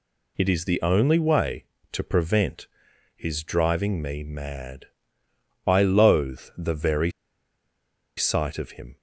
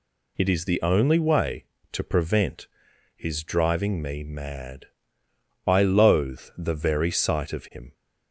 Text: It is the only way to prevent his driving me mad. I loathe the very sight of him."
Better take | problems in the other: second | pauses between "prevent" and "his"; noticeable; at 2.6 s; 0.48 s long; noticeable in the second // pauses between "loathe" and "the"; slight; at 6.4 s; 0.16 s long; slight in the second // pauses between "very" and "sight"; at 7.1 s; 1.0 s long

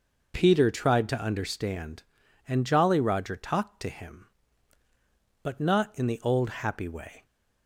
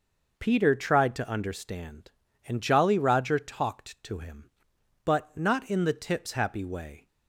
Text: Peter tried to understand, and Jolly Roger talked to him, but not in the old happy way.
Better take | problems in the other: first | says "tips" for "old"; at 5.9 s

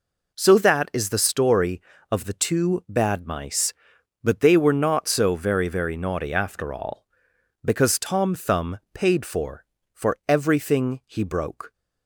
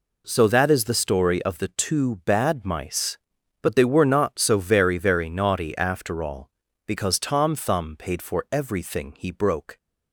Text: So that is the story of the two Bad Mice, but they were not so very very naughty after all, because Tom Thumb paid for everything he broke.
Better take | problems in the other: second | says "for" twice; at 9.9 s

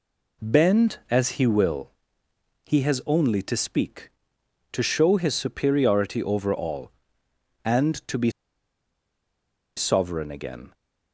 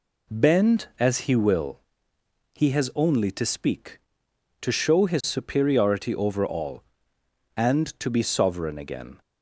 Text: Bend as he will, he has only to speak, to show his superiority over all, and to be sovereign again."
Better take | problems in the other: second | pauses between "be" and "sovereign"; strong; at 8.3 s; 1.4 s long

